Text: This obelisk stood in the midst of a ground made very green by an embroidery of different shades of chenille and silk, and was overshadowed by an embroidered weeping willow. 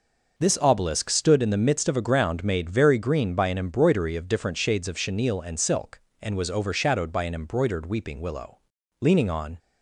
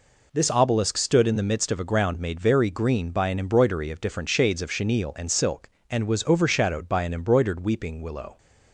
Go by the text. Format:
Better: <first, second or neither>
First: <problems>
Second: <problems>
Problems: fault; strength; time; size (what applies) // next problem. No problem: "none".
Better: second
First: goes on to say "Leaning on"; from 9.0 s on; 0.58 s long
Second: none